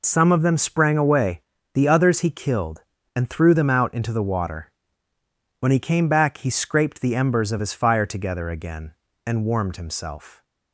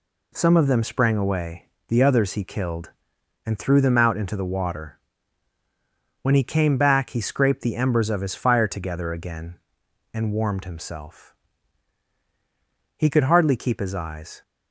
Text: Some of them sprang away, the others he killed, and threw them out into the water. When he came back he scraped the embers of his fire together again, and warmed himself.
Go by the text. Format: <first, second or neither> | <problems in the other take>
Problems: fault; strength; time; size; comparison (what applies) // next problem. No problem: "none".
first | goes on to say "He could hardly keep his eyes"; from 12.9 s on; 1.4 s long